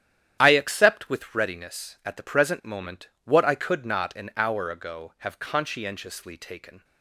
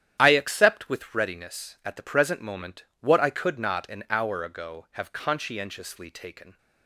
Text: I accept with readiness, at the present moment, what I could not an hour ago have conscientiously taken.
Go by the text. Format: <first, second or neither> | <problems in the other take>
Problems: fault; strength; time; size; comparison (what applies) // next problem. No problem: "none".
neither | starts louder than the rest; strong; the same in both